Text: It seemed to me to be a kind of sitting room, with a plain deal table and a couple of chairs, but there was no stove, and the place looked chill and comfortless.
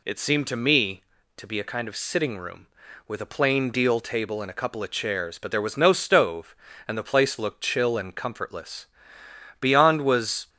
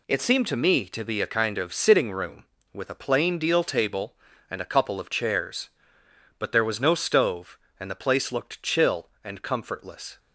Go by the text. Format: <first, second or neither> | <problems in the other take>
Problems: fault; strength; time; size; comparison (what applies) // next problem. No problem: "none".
second | goes on to say "Beyond was"; noticeable; from 9.6 s on; 0.88 s long